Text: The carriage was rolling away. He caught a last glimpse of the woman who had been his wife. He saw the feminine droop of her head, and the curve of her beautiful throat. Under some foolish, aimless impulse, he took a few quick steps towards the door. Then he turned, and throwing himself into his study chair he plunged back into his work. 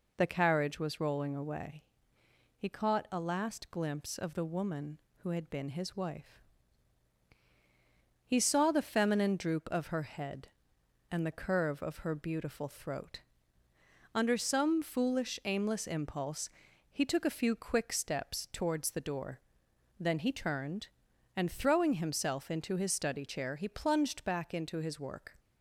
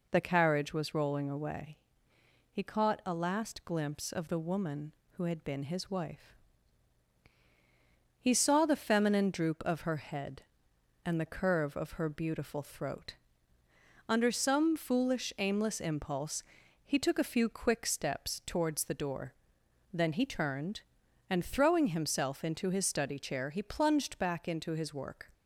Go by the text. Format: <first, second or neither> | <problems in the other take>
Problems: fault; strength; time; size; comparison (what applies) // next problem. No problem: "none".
neither | none